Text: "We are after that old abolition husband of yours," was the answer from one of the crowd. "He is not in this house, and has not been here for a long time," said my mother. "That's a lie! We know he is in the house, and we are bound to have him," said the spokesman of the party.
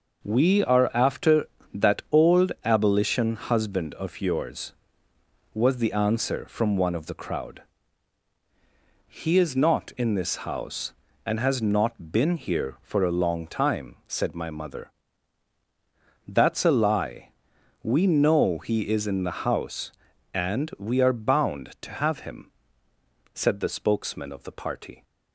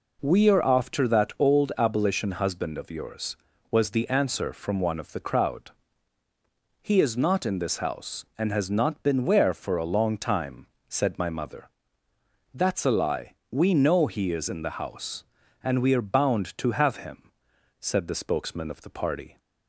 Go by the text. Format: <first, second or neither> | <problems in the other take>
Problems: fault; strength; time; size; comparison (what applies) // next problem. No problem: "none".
first | says "where" for "here"; at 9.2 s